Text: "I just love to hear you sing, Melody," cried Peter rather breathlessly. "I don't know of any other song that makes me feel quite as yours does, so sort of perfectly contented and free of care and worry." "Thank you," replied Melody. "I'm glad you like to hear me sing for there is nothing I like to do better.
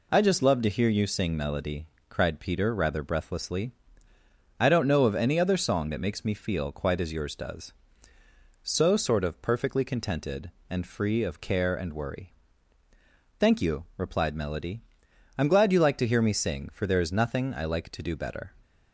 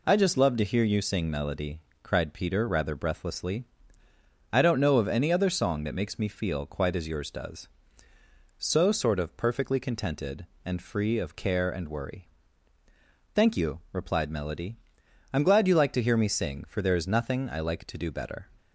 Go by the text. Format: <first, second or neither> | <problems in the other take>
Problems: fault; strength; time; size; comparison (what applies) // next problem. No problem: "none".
neither | none